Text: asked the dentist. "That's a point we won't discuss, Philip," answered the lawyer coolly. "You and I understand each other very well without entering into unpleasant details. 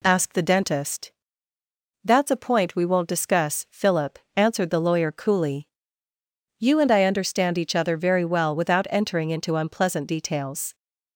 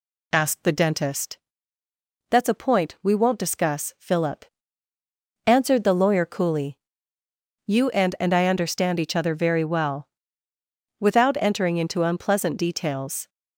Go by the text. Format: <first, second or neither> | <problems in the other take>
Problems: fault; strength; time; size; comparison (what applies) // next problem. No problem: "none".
first | says "and" twice; at 8.1 s // pauses between "well" and "without"; noticeable; at 10.0 s; 0.90 s long